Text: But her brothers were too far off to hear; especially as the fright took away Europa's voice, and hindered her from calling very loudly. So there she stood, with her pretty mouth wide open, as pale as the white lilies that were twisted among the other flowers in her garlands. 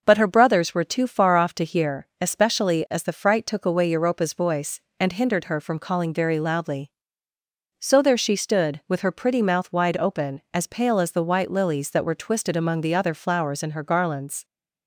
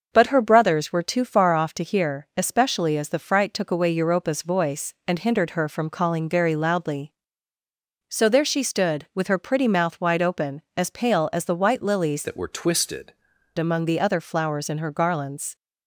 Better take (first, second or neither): first